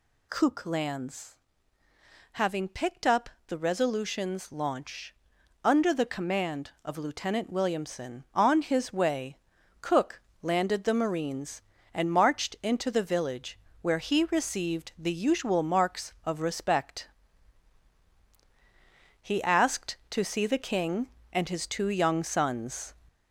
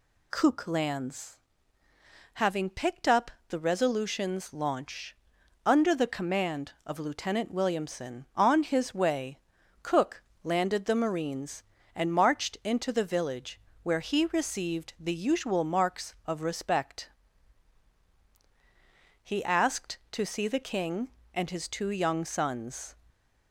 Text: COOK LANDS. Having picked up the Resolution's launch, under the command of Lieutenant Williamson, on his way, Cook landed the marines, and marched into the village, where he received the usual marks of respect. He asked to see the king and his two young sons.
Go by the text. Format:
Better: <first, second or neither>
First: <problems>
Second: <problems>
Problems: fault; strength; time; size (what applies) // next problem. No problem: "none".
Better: second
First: gets louder; slight; throughout; 2.5 dB // pauses between "up" and "the"; slight; at 3.2 s; 0.20 s long // pauses between "Cook" and "landed"; slight; at 10.2 s; 0.20 s long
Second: pauses between "up" and "the"; slight; at 3.2 s; 0.20 s long // pauses between "Cook" and "landed"; slight; at 10.2 s; 0.20 s long